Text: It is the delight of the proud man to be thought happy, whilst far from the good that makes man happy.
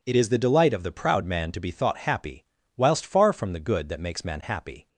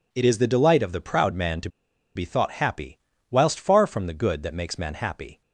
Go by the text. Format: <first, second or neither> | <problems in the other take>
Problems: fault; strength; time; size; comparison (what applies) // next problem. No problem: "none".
first | pauses between "to" and "be"; noticeable; at 1.6 s; 0.46 s long